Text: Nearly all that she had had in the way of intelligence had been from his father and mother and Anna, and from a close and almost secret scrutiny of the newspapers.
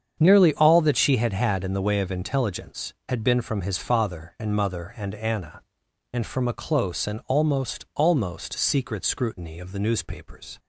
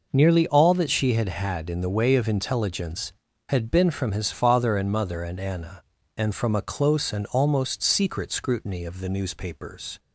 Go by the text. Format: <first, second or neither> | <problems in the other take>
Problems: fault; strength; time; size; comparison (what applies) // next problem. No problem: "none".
second | starts louder than the rest; strong; until 1.2 s; 7.5 dB // says "almost" twice; at 7.9 s